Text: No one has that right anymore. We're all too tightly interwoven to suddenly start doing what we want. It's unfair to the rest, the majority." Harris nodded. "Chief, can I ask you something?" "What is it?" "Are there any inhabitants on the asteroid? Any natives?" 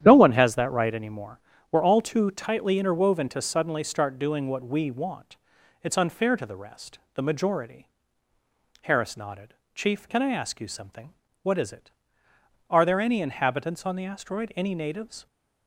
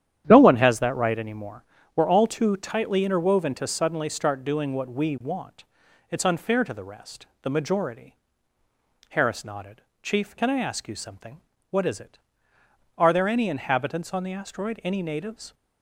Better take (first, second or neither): neither